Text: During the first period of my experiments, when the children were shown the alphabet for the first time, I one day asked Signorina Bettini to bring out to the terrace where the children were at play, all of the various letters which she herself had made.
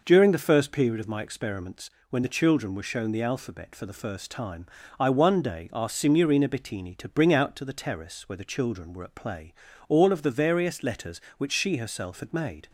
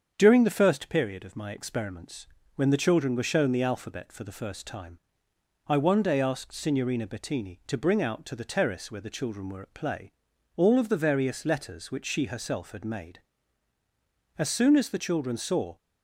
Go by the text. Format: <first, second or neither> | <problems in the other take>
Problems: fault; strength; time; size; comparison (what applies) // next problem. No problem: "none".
first | starts louder than the rest; strong; until 1.1 s; 7.5 dB // goes on to say "As soon as the children saw"; from 14.3 s on; 1.4 s long